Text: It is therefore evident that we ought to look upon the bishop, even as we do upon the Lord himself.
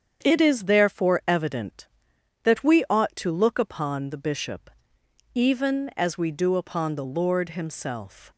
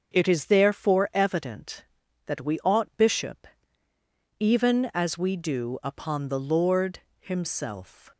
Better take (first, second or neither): first